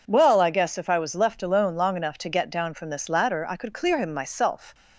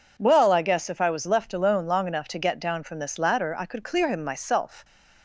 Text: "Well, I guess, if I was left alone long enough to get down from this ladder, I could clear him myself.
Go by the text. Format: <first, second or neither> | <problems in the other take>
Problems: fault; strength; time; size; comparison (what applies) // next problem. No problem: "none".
neither | none